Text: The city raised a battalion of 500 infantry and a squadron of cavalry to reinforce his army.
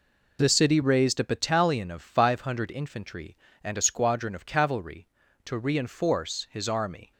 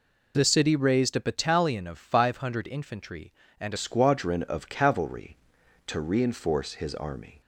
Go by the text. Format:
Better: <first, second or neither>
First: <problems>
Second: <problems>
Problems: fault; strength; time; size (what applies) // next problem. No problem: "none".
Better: first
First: none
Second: changes voice at "squadron"; from 3.7 s on; 3.7 s long